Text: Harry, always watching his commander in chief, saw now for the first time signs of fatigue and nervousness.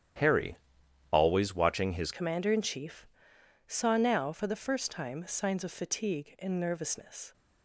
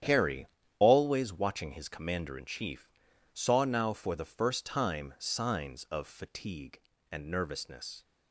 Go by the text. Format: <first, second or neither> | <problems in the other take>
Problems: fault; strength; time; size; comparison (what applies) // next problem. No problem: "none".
second | starts louder than the rest; strong; until 1.7 s; 10.5 dB; strong in the second // changes voice at "commander"; from 2.1 s on; 5.2 s long